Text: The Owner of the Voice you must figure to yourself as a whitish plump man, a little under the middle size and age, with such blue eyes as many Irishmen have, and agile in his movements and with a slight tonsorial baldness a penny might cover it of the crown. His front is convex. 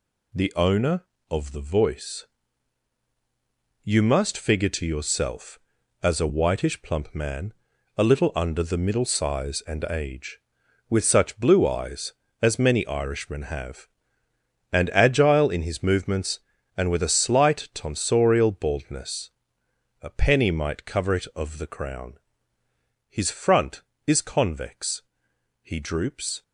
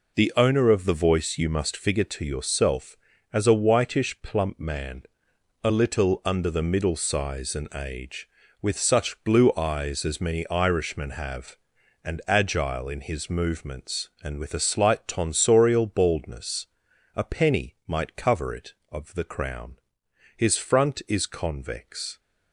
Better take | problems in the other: second | pauses between "Voice" and "you"; strong; at 2.2 s; 1.5 s long // pauses between "baldness" and "a"; noticeable; at 19.3 s; 0.72 s long; noticeable in the second // goes on to say "He droops"; noticeable; from 25.6 s on; 0.80 s long

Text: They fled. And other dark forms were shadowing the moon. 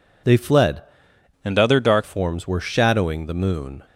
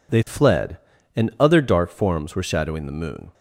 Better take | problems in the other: second | changes voice from "And" to "dark"; from 1.4 to 2.0 s; 0.6 s long

